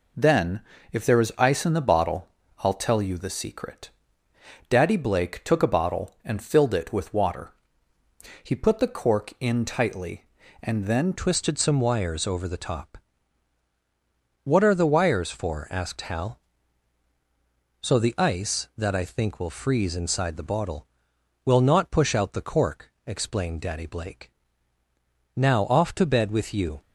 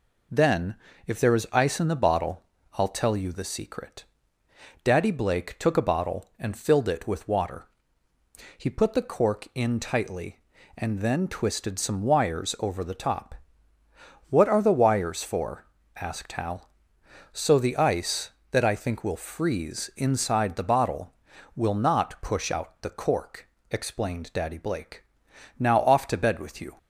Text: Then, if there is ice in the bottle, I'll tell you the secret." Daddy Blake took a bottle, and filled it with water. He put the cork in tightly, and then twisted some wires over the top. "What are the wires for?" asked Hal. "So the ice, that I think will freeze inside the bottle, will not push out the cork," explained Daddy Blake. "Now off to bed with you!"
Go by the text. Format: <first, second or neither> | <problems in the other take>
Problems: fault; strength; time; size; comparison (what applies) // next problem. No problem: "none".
second | changes voice at "twisted"; from 11.1 s on; 15.7 s long